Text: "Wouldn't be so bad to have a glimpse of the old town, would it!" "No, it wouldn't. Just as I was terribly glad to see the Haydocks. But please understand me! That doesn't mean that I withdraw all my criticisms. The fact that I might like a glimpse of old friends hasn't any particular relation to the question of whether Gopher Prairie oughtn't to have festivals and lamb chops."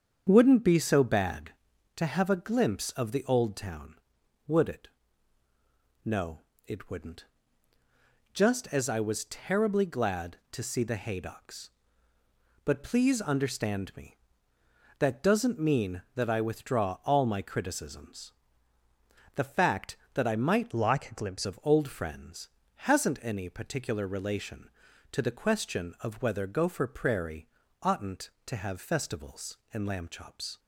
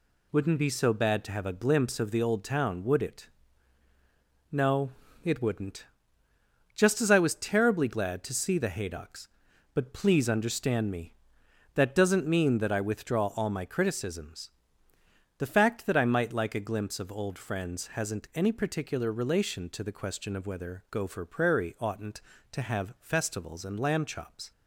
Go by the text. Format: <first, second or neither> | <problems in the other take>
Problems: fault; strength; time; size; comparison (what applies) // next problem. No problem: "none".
second | starts louder than the rest; strong; until 1.2 s; 7.5 dB // changes voice from "like" to "glimpse"; from 20.7 to 21.4 s; 0.7 s long // pauses between "friends" and "hasn't"; slight; at 22.4 s; 0.36 s long // pauses between "Prairie" and "oughtn't"; slight; at 27.4 s; 0.34 s long